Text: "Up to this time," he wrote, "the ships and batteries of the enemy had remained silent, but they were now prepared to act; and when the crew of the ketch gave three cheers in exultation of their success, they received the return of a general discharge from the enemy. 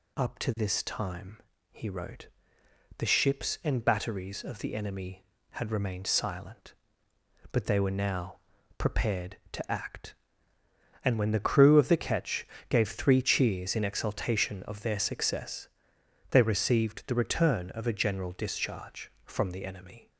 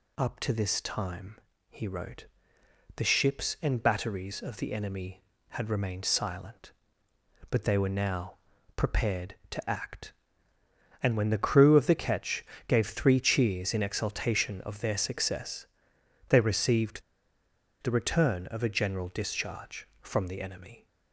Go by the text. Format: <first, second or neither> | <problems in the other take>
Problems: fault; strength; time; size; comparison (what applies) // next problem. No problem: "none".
first | pauses between "now" and "prepared"; at 8.3 s; 0.40 s long; also in the first // pauses between "ketch" and "gave"; slight; at 12.4 s; 0.22 s long; slight in the first // pauses between "received" and "the"; noticeable; at 17.0 s; 0.82 s long